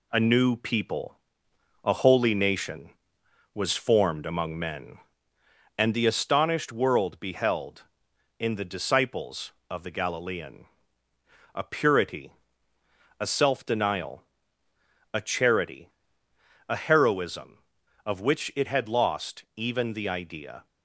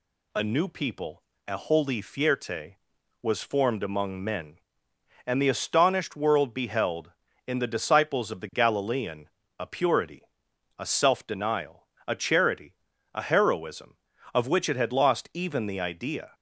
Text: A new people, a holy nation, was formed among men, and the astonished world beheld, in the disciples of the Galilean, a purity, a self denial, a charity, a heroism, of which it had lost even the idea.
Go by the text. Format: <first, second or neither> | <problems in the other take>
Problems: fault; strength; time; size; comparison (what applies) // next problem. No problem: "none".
first | says "fierte" for "nation"; at 2.0 s